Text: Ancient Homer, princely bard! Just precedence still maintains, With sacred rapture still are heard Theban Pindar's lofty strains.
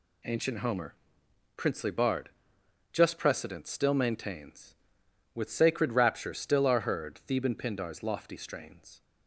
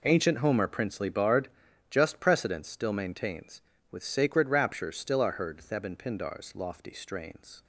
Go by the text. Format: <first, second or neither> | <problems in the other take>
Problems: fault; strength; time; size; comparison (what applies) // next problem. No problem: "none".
neither | none